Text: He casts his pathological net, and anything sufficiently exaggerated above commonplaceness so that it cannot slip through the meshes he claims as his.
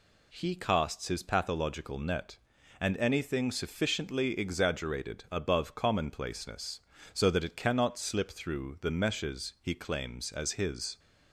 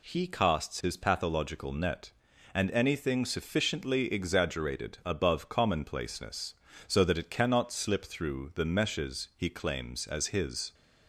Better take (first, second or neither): neither